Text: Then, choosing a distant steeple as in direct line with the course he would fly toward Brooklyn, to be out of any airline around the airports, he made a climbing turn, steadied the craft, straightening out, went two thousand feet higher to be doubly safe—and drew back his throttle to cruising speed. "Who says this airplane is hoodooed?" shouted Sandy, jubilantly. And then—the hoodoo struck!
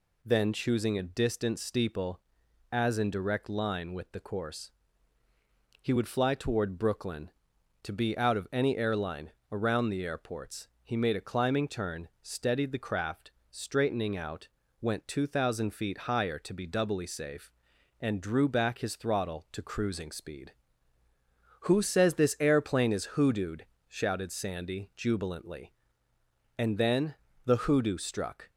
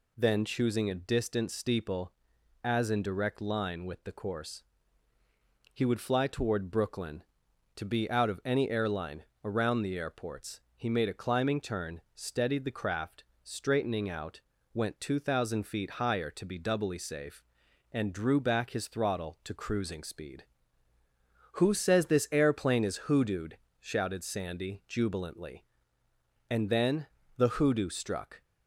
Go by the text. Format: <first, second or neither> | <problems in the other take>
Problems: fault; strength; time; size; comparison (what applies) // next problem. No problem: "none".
neither | pauses between "course" and "he"; the same in both // pauses between "airline" and "around"; slight; the same in both